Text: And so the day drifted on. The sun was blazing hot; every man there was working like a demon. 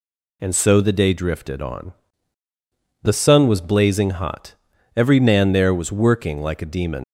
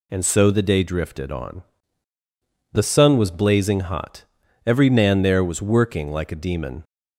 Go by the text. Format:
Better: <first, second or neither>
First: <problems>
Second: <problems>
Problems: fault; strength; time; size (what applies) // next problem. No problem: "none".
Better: second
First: leaves "demon" unfinished; at 7.0 s; 100 ms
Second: none